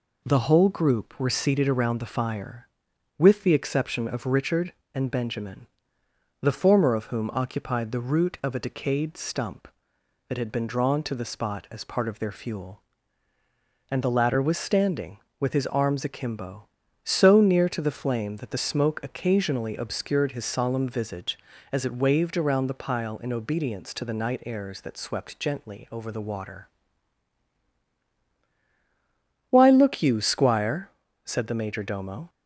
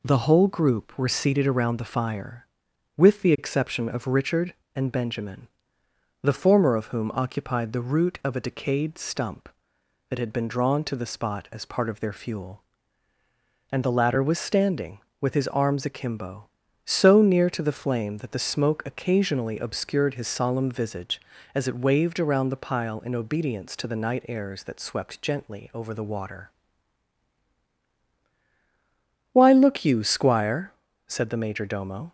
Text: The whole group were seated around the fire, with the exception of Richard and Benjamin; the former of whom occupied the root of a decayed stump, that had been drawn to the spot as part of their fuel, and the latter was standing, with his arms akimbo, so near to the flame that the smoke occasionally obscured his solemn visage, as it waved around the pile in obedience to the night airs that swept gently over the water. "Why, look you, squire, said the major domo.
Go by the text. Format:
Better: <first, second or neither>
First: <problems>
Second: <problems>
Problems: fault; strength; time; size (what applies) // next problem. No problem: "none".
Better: neither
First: none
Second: none